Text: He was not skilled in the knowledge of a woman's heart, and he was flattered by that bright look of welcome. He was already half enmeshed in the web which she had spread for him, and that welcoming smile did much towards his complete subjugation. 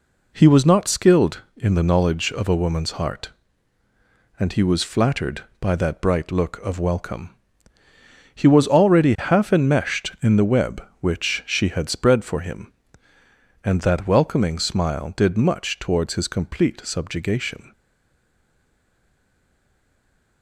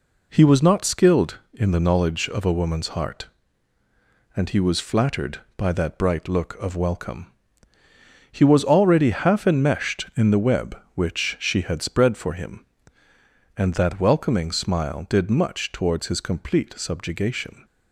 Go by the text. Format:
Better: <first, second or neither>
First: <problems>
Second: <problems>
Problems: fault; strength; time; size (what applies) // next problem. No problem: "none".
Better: second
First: stays silent after the last word; strong; from 17.7 s on; 2.7 s long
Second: none